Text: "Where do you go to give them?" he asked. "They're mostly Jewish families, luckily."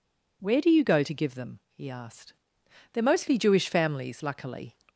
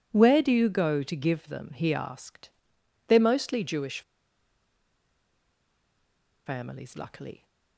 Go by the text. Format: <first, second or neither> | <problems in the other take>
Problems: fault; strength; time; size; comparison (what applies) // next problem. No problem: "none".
first | pauses between "Jewish" and "families"; strong; at 4.0 s; 2.4 s long